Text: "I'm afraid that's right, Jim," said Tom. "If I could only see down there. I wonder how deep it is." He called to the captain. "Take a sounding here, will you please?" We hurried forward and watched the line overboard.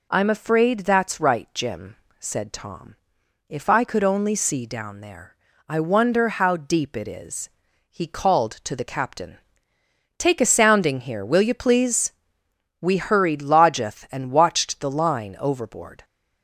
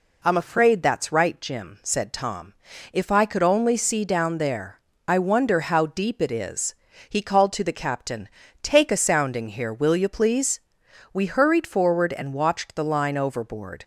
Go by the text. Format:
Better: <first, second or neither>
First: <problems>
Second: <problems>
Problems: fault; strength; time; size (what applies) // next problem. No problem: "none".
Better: second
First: says "lodgeth" for "forward"; at 13.4 s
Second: none